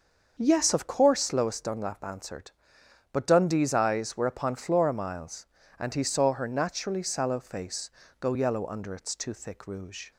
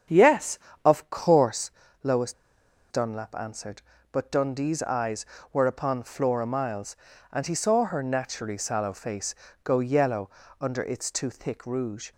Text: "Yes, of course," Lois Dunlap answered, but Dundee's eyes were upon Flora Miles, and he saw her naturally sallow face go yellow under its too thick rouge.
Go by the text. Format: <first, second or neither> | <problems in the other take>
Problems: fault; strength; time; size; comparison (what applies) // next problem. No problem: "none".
first | starts louder than the rest; strong; until 1.3 s; 8 dB; also in the first // pauses between "Lois" and "Dunlap"; noticeable; at 2.3 s; 0.58 s long // pauses between "face" and "go"; slight; at 9.3 s; 0.30 s long; slight in the first // pauses between "yellow" and "under"; slight; at 10.2 s; 0.32 s long